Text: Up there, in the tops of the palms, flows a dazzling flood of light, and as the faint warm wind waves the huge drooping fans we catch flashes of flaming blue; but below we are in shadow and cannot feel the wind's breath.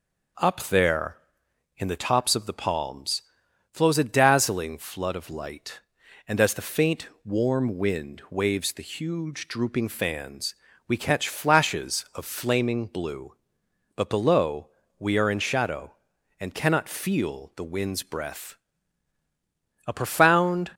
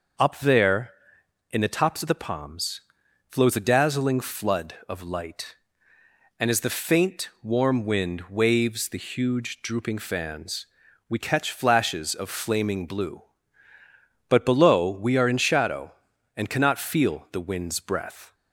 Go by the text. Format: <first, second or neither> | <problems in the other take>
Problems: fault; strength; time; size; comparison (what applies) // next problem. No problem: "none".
second | pauses between "faint" and "warm"; slight; at 7.0 s; 0.16 s long // pauses between "fans" and "we"; slight; at 10.5 s; 0.35 s long; also in the second // pauses between "below" and "we"; slight; at 14.6 s; 0.30 s long // goes on to say "A profound"; noticeable; from 19.8 s on; 0.86 s long